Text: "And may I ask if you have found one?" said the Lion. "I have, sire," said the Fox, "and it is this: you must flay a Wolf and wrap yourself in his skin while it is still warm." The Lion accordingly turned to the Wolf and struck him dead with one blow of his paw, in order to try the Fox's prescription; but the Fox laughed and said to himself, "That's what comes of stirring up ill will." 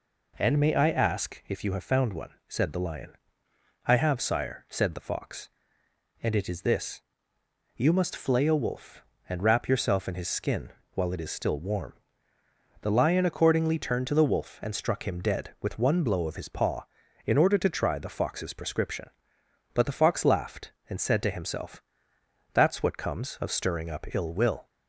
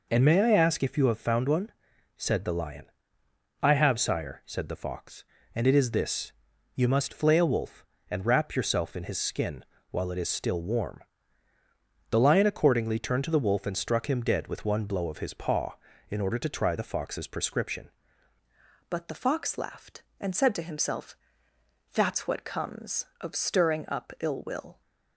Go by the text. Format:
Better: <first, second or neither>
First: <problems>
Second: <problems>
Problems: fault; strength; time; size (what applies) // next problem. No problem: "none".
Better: first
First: pauses between "skin" and "while"; slight; at 10.7 s; 0.22 s long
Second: pauses between "skin" and "while"; slight; at 9.6 s; 0.26 s long // changes voice at "but"; from 18.8 s on; 6.0 s long